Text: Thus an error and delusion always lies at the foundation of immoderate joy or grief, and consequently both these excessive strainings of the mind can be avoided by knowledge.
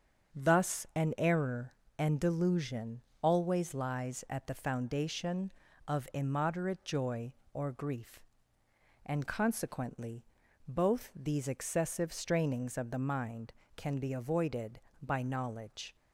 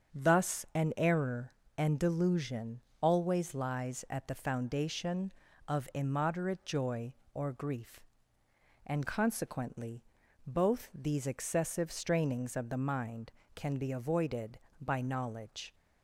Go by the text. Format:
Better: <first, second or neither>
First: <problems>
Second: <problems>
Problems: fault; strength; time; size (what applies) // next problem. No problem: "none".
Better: neither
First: starts louder than the rest; until 1.4 s; 7 dB // pauses between "delusion" and "always"; slight; at 3.0 s; 0.20 s long // pauses between "consequently" and "both"; at 10.2 s; 0.44 s long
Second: starts louder than the rest; strong; until 1.2 s; 7.5 dB // pauses between "delusion" and "always"; slight; at 2.8 s; 0.20 s long // pauses between "consequently" and "both"; at 10.0 s; 0.44 s long